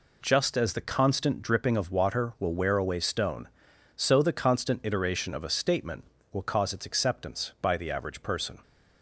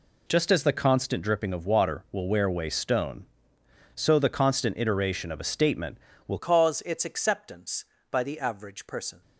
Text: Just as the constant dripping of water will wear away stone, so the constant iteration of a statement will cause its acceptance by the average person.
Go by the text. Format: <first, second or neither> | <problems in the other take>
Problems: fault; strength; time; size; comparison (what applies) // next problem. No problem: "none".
first | changes voice at "cause"; from 6.3 s on; 2.9 s long